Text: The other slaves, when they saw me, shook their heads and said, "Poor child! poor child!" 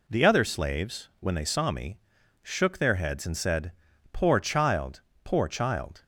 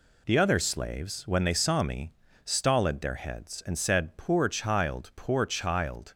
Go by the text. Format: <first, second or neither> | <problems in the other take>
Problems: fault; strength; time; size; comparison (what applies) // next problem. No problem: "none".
first | says "stolid" for "shook"; at 2.4 s